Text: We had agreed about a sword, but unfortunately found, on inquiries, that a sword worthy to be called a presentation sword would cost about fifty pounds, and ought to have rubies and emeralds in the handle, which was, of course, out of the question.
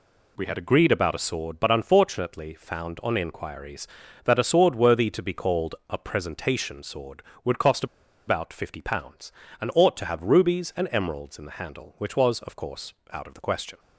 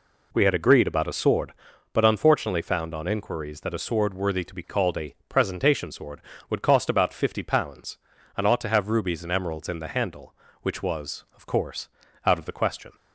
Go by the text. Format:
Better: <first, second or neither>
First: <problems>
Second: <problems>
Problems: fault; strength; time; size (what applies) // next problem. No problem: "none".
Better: second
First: pauses between "cost" and "about"; at 7.8 s; 0.42 s long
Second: none